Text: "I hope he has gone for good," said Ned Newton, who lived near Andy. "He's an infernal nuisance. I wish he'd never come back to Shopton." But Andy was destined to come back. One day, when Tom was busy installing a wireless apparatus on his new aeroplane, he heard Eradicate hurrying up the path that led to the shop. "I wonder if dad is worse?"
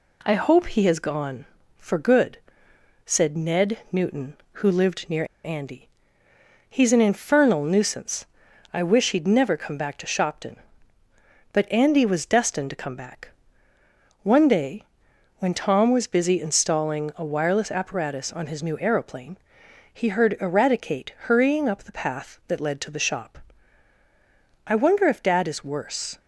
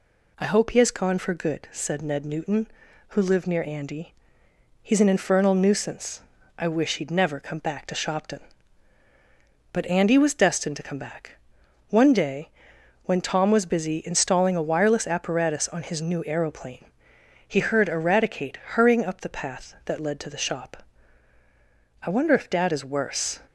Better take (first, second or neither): second